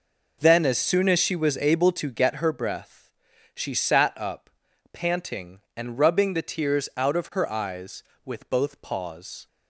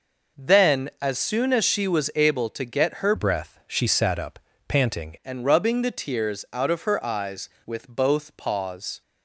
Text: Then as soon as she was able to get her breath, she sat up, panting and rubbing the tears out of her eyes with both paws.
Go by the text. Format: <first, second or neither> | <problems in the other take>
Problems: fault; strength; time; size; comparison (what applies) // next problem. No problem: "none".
first | changes voice from "breath" to "panting"; from 3.1 to 5.1 s; 2.0 s long